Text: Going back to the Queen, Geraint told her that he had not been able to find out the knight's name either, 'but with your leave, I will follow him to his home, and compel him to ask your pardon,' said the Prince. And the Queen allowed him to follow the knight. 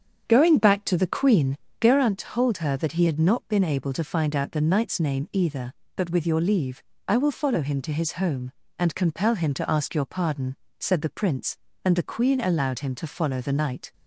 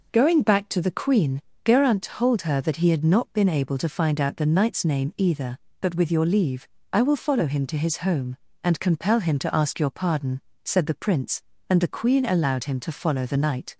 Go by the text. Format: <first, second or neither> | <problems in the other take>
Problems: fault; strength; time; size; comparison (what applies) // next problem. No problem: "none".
second | starts louder than the rest; strong; until 2.0 s; 7.5 dB